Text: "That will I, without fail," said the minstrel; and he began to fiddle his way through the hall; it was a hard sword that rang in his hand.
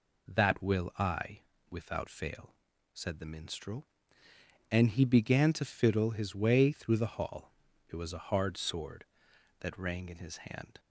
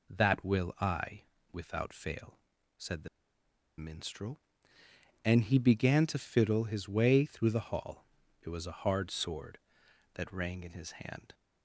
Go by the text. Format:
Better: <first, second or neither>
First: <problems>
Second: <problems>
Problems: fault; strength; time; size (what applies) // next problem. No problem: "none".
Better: first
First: none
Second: pauses between "the" and "minstrel"; noticeable; at 3.0 s; 0.71 s long